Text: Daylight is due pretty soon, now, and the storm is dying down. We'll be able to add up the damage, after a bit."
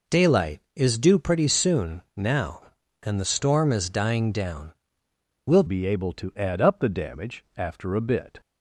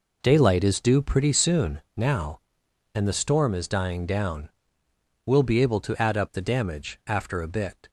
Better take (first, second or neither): second